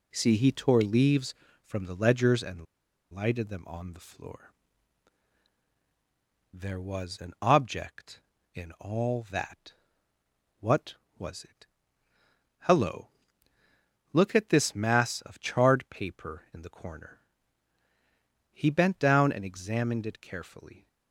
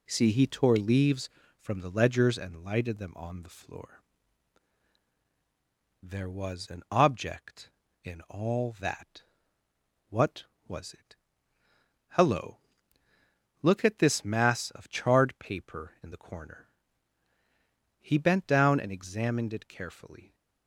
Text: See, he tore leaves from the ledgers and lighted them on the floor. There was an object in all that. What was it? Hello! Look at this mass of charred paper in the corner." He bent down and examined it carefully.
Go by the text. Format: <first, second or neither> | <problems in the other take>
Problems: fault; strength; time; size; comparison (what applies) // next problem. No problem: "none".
second | pauses between "and" and "lighted"; noticeable; at 2.6 s; 0.48 s long